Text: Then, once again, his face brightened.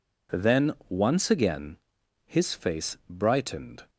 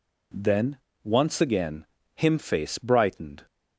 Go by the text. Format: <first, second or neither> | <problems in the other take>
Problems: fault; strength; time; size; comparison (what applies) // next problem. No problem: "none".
first | says "him" for "his"; at 2.1 s